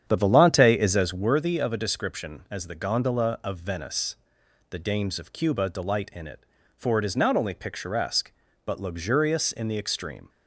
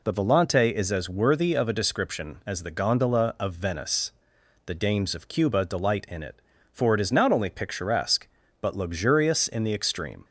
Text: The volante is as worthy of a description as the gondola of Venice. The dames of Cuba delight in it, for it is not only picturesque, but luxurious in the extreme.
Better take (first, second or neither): second